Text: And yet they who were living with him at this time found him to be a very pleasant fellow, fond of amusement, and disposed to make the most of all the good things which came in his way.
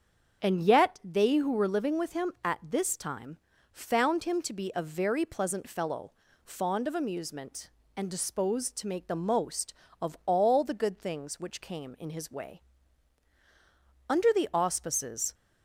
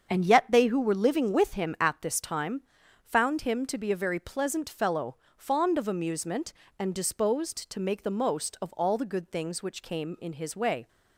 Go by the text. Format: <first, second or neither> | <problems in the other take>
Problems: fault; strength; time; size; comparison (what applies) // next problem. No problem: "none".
second | starts louder than the rest; strong; until 1.4 s; 7 dB; strong in the second // pauses between "time" and "found"; slight; at 3.3 s; 0.34 s long; also in the second // goes on to say "Under the auspices"; noticeable; from 14.0 s on; 1.2 s long